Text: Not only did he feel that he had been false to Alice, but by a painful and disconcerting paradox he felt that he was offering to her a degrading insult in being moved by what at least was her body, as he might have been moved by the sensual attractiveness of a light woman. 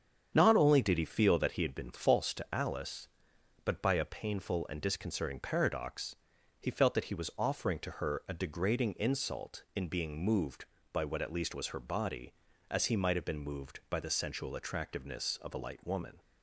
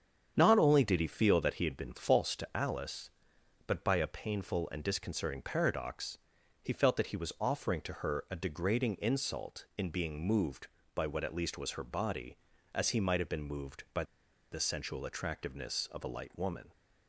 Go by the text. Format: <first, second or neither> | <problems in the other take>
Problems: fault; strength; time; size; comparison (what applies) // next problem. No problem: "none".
first | starts louder than the rest; strong; until 1.3 s; 8 dB; strong in the first // pauses between "paradox" and "he"; at 6.1 s; 0.44 s long; also in the first // pauses between "by" and "the"; noticeable; at 14.0 s; 0.48 s long